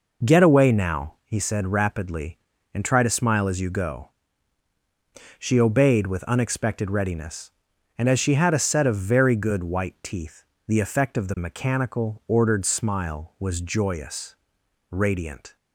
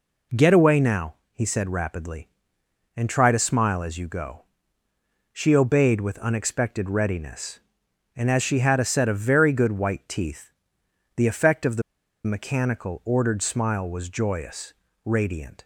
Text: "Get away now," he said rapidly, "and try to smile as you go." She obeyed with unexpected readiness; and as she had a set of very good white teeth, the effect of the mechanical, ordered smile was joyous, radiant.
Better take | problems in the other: first | pauses between "the" and "mechanical"; at 11.8 s; 0.43 s long

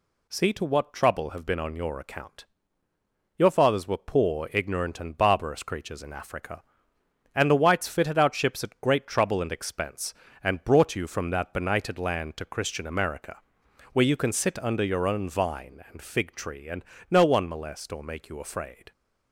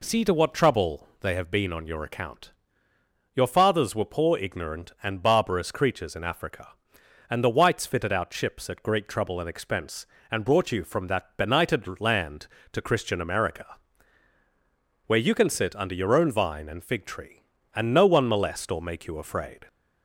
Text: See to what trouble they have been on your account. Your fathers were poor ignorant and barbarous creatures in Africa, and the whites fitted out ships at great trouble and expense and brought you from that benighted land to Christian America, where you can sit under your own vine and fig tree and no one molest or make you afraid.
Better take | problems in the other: second | skips "they"; at 1.2 s // pauses between "and" and "no"; slight; at 16.8 s; 0.26 s long

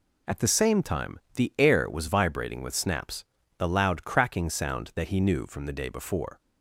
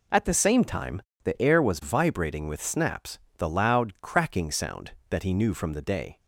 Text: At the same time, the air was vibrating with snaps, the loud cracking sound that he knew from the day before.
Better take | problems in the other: first | stops before "before"; at 6.1 s

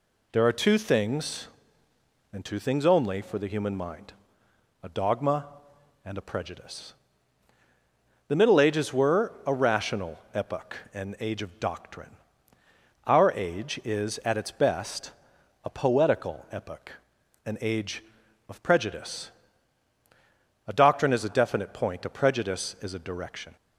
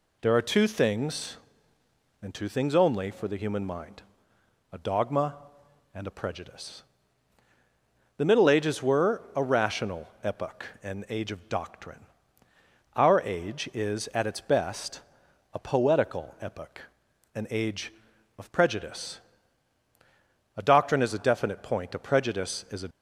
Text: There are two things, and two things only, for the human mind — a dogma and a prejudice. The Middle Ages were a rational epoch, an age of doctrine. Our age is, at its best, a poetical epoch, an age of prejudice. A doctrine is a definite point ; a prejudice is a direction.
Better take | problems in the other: first | stops before "direction"; at 22.9 s

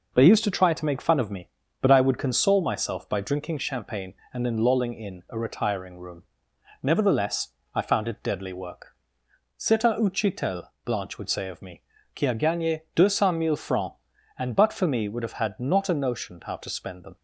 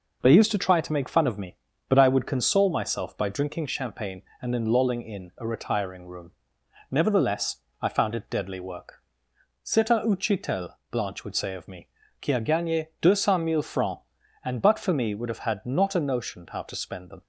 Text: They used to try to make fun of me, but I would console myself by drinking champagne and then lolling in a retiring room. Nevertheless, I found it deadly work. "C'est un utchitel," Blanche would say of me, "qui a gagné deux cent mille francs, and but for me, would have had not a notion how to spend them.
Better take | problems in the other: neither | none

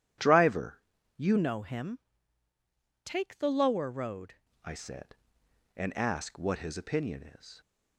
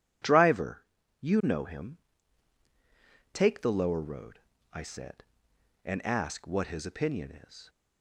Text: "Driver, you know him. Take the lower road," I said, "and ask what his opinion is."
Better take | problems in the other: second | starts louder than the rest; strong; until 1.5 s; 11 dB // changes voice from "know" to "road"; from 1.3 to 4.3 s; 3.0 s long

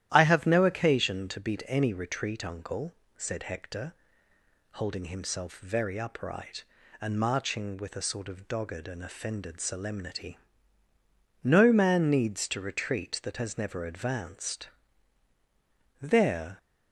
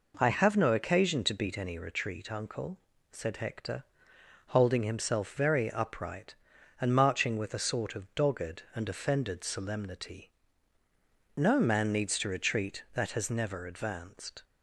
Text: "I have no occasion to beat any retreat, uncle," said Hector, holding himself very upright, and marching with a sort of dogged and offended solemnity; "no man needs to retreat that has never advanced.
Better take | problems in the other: second | starts louder than the rest; strong; until 1.1 s; 12 dB // goes on to say "There"; from 16.0 s on; 0.56 s long

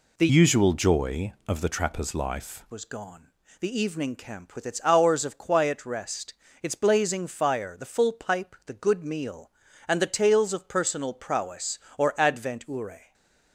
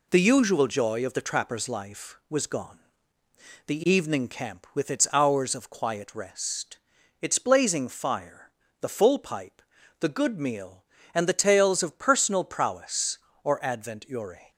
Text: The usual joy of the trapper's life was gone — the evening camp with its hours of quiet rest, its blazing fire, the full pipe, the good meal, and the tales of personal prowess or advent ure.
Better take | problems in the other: second | changes voice from "usual" to "life"; from 0.2 to 2.6 s; 2.4 s long // stays silent after the last word; slight; from 13.0 s on; 0.5 s long

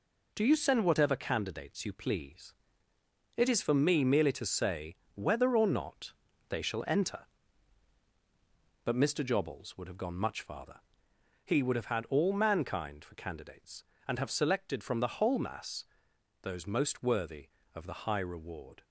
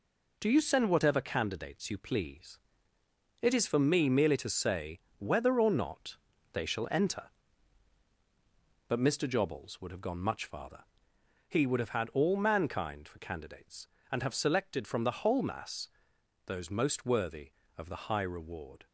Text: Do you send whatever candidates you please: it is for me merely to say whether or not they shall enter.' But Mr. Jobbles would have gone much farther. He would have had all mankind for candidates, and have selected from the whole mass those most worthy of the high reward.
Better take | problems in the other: neither | pauses between "say" and "whether"; slight; the same in both // pauses between "not" and "they"; the same in both // pauses between "mass" and "those"; noticeable; the same in both

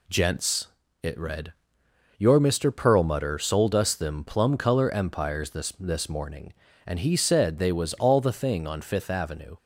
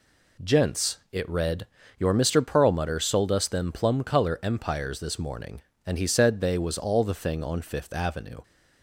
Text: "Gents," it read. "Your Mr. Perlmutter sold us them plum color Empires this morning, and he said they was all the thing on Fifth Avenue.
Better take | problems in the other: second | says "this" twice; at 5.7 s

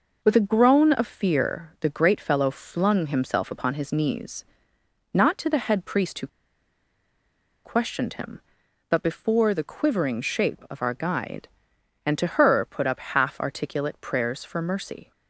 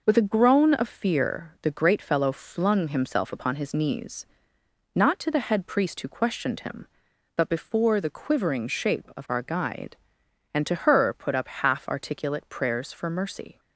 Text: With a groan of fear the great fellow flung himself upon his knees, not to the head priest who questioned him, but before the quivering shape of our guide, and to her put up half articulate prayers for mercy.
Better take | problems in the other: second | pauses between "who" and "questioned"; strong; at 6.2 s; 1.3 s long

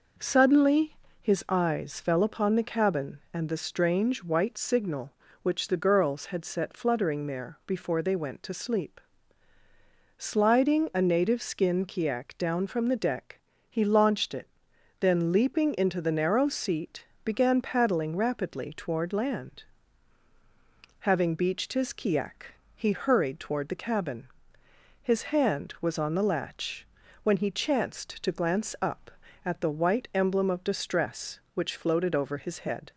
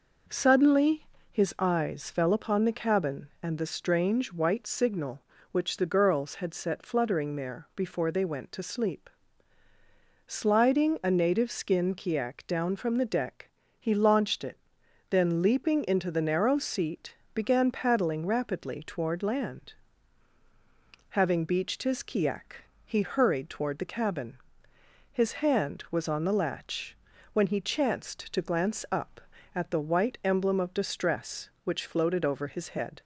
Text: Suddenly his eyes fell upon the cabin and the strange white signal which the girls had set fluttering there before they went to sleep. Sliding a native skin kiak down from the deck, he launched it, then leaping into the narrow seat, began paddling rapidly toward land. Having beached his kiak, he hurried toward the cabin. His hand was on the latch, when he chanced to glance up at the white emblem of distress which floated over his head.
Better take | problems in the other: neither | pauses between "Suddenly" and "his"; slight; the same in both

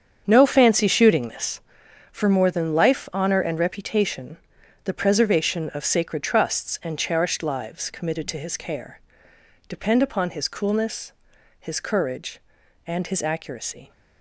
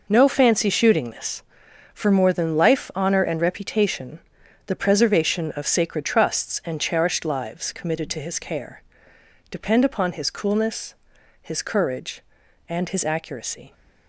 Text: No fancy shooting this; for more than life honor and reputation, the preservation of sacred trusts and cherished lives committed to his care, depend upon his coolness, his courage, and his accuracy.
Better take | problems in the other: second | starts louder than the rest; strong; until 1.8 s; 7.5 dB

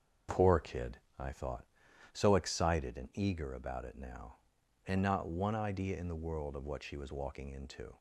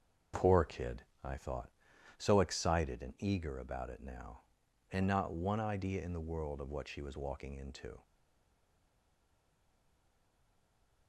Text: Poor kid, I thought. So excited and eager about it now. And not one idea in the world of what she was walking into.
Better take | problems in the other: first | starts louder than the rest; until 1.5 s; 6.5 dB; also in the first // stays silent after the last word; strong; from 8.0 s on; 3.0 s long

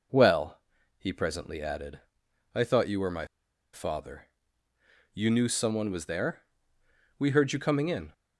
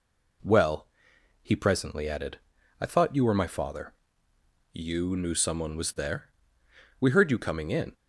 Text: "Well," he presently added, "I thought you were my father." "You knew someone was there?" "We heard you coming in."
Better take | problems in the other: second | pauses between "my" and "father"; noticeable; at 3.2 s; 0.46 s long

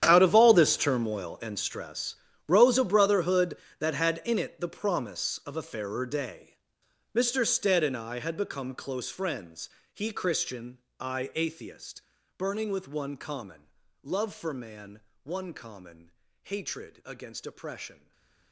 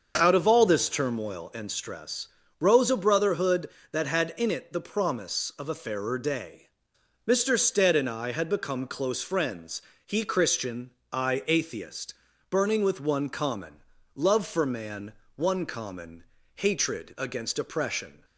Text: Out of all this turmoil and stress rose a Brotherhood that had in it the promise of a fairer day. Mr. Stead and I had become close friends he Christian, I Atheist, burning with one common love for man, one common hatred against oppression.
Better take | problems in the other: second | gets quieter; strong; throughout; 18 dB // starts louder than the rest; strong; until 1.0 s; 10 dB; also in the second // pauses between "stress" and "rose"; slight; at 2.1 s; 0.30 s long; slight in the second // pauses between "friends" and "he"; slight; at 9.6 s; 0.24 s long; slight in the second // pauses between "common" and "love"; slight; at 13.6 s; 0.32 s long; slight in the second // pauses between "common" and "hatred"; slight; at 16.1 s; 0.30 s long; slight in the second // stays silent after the last word; slight; from 17.9 s on; 0.6 s long

